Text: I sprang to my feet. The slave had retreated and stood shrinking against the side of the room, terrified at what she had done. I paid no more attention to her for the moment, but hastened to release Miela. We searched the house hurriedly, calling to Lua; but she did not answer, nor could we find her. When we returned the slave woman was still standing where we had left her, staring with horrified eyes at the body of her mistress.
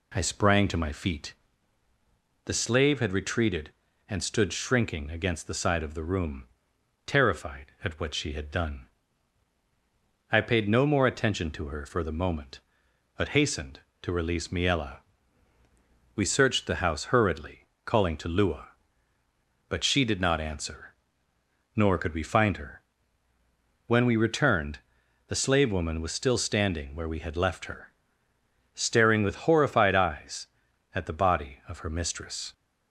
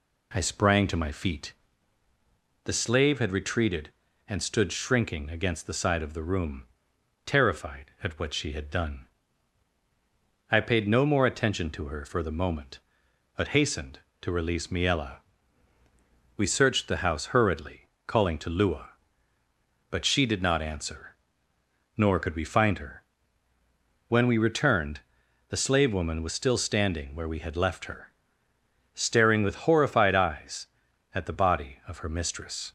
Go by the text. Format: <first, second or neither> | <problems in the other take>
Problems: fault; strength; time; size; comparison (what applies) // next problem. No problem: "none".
neither | pauses between "returned" and "the"; noticeable; the same in both